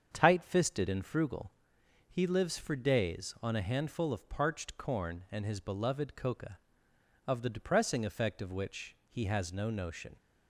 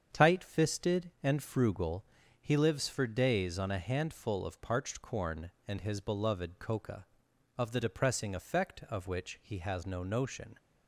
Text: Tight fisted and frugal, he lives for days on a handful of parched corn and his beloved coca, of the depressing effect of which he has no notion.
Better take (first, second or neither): neither